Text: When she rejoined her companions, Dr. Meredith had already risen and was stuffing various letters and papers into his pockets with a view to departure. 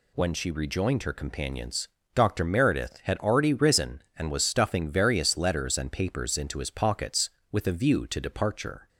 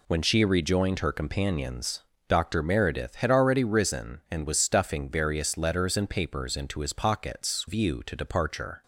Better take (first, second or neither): first